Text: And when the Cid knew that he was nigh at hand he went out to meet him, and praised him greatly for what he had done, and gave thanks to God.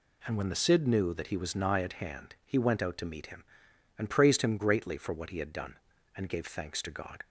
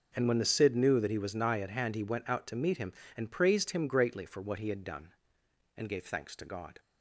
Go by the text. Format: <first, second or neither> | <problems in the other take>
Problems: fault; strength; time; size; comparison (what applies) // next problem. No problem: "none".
neither | none